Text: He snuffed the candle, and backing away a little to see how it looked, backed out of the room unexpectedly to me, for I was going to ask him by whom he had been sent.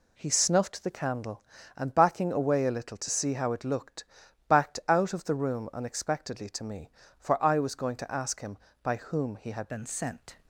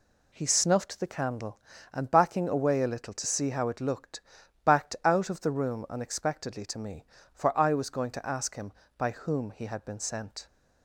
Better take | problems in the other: second | changes voice at "been"; from 9.6 s on; 0.7 s long

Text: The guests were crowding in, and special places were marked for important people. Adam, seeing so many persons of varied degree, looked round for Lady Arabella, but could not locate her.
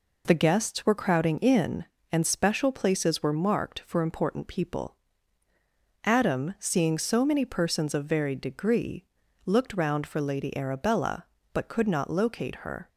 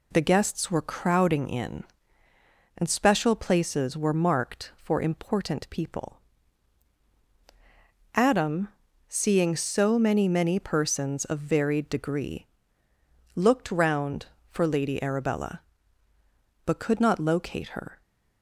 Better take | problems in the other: first | says "many" twice; at 10.2 s

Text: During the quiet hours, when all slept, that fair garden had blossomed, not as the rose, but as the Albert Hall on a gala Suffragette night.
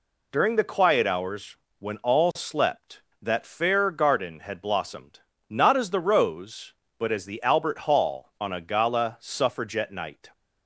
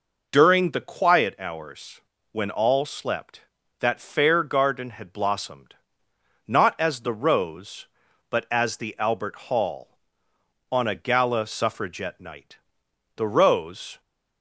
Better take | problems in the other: first | goes on to say "The rose"; noticeable; from 13.1 s on; 0.84 s long

